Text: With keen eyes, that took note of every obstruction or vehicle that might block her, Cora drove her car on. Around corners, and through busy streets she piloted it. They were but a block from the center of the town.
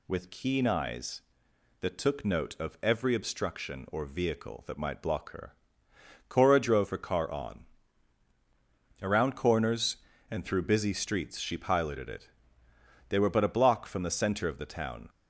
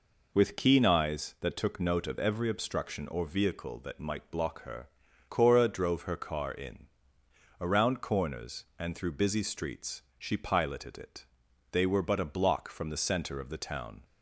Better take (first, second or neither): first